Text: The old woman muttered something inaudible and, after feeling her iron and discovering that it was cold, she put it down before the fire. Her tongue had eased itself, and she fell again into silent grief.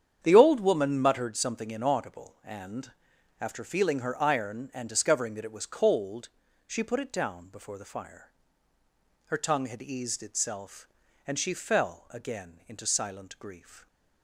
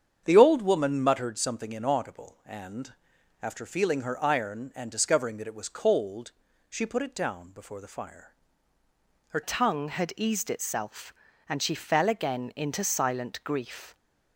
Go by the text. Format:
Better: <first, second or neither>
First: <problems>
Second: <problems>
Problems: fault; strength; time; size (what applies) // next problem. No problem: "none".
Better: first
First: starts louder than the rest; strong; until 1.2 s; 8.5 dB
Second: starts louder than the rest; strong; until 1.2 s; 8 dB // changes voice at "tongue"; from 9.4 s on; 4.5 s long